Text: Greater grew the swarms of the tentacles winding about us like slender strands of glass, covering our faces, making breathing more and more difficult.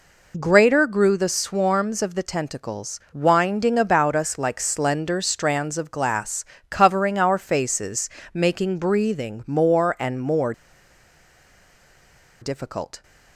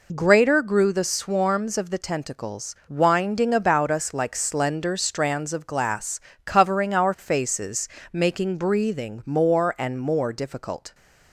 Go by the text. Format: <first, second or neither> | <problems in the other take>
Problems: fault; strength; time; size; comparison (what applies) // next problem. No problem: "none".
second | pauses between "more" and "difficult"; strong; at 10.5 s; 1.8 s long